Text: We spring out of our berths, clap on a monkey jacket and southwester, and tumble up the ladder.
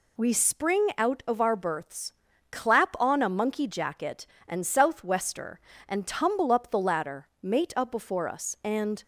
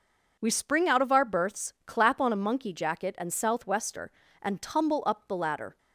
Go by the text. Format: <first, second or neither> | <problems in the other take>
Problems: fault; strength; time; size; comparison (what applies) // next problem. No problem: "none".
second | goes on to say "Mate up before us and"; from 7.4 s on; 1.6 s long